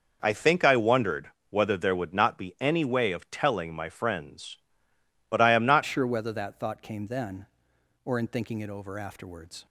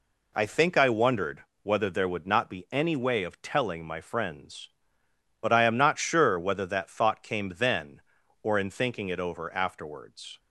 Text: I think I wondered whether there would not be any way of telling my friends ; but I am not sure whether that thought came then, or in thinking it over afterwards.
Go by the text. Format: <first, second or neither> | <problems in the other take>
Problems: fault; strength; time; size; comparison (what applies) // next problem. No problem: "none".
second | pauses between "wondered" and "whether"; slight; at 1.3 s; 0.18 s long; slight in the second // changes voice at "sure"; from 5.8 s on; 3.8 s long